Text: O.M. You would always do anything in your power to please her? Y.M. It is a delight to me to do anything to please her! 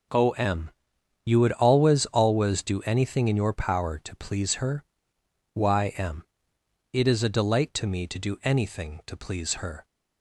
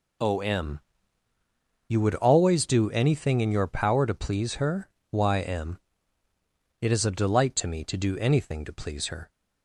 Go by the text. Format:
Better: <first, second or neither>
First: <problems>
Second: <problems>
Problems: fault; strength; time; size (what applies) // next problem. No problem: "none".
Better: second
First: says "always" twice; at 2.0 s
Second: none